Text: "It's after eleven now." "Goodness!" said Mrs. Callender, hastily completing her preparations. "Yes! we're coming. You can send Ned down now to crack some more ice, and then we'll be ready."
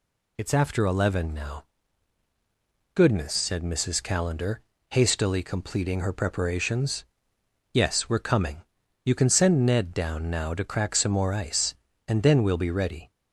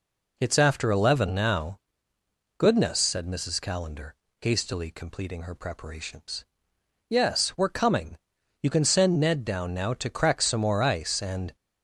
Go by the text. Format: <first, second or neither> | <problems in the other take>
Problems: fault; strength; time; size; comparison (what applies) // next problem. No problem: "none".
first | stops before "then we'll be ready"; at 11.5 s